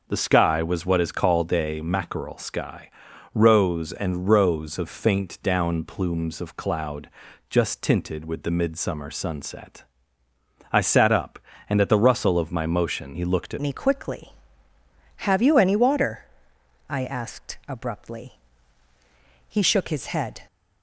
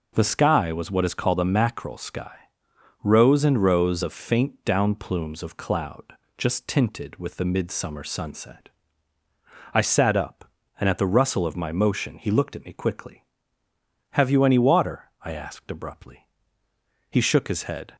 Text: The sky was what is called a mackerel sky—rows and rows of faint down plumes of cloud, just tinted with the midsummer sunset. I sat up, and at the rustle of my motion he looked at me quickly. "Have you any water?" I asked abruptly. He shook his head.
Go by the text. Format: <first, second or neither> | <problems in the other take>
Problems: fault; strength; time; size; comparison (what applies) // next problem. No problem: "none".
second | changes voice at "me"; from 13.6 s on; 6.8 s long